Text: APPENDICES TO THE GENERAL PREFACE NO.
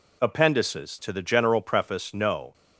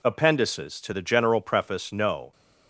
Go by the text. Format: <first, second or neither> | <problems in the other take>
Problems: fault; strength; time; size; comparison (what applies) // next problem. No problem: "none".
neither | none